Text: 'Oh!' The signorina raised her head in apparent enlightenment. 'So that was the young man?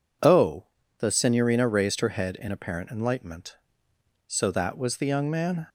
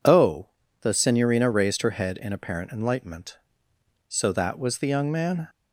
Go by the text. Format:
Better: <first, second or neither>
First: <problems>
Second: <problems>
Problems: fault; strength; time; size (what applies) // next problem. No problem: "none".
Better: neither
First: none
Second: none